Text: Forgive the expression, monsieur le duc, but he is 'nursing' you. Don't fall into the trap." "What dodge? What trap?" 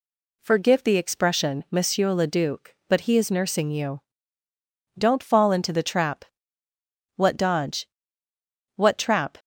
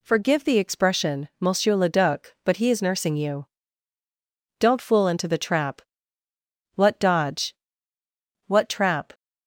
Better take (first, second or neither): first